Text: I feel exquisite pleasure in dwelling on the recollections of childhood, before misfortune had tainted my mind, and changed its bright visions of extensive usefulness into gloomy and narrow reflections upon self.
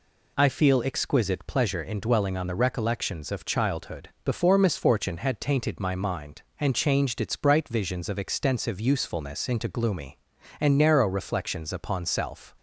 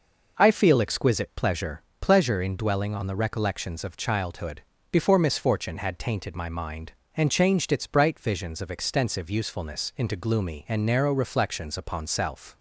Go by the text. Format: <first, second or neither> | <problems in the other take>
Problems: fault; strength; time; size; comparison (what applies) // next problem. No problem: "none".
first | says "pleasure" twice; at 2.0 s